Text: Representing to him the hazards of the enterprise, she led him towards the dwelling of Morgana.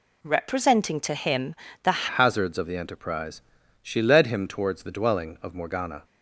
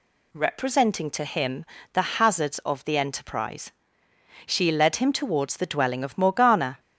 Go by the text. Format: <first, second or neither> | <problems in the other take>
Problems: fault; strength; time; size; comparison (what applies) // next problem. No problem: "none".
second | pauses between "him" and "the"; slight; at 1.5 s; 0.26 s long; slight in the second // changes voice at "hazards"; from 2.0 s on; 4.0 s long